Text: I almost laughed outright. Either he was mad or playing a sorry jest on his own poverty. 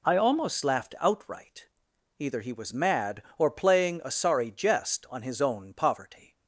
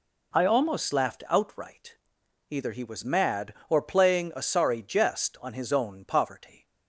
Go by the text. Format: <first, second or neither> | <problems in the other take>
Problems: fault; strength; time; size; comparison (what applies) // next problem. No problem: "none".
neither | none